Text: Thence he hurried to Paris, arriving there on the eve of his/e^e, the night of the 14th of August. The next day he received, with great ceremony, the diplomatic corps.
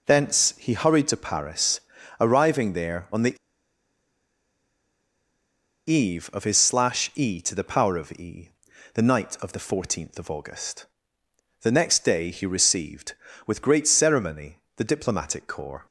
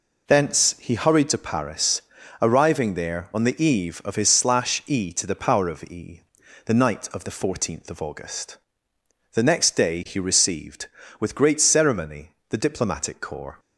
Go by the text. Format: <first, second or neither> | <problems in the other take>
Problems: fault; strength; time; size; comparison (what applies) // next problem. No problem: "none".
second | pauses between "the" and "eve"; strong; at 3.3 s; 2.5 s long